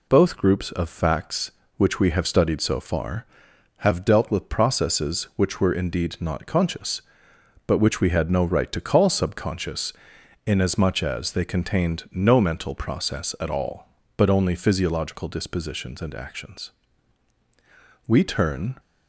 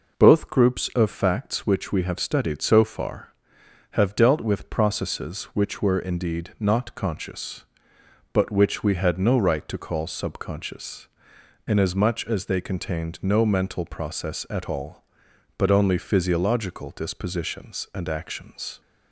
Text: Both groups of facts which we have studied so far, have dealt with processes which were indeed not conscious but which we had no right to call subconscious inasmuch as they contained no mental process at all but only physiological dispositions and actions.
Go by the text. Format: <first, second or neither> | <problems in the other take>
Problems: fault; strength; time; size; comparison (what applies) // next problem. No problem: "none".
second | pauses between "subconscious" and "inasmuch"; noticeable; at 9.9 s; 0.54 s long; noticeable in the second // goes on to say "We turn"; noticeable; from 18.0 s on; 0.72 s long